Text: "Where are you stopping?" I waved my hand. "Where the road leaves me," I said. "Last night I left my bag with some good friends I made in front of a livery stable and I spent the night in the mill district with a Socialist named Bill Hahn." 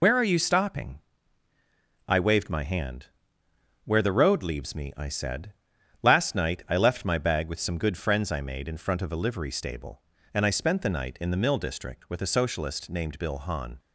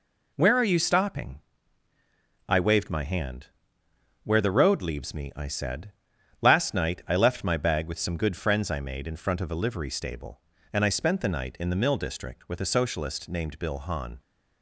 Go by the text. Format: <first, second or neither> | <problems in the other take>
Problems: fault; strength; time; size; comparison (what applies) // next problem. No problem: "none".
second | loses the start of "Where"; at 0.0 s; 75 ms